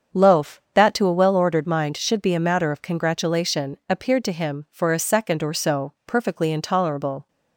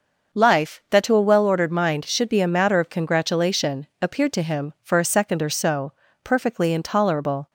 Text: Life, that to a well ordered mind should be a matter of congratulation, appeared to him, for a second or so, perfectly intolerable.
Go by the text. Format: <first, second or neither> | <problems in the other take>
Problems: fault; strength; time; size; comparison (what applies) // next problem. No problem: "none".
second | starts louder than the rest; strong; until 1.2 s; 7 dB; also in the second // says "Loaf" for "Life"; at 0.1 s